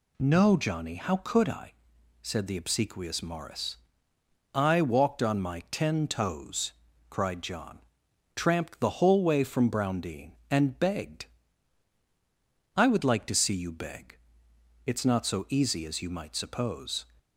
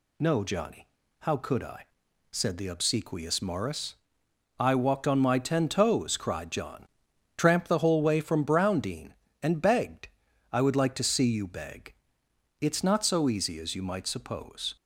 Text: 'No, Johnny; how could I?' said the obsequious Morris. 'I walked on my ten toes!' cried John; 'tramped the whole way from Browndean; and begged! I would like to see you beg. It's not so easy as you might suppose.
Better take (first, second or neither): neither